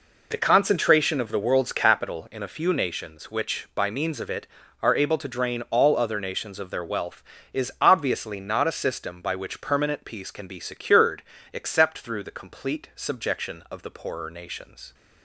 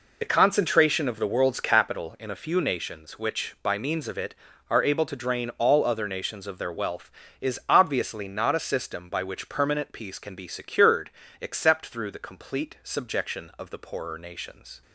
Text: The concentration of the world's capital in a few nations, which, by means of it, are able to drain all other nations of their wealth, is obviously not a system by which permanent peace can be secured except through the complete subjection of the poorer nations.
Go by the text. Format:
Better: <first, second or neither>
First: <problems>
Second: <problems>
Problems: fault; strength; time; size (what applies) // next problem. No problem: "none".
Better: first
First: pauses between "secured" and "except"; slight; at 11.2 s; 0.30 s long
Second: loses the start of "The"; at 0.2 s; 25 ms // pauses between "secured" and "except"; slight; at 11.0 s; 0.30 s long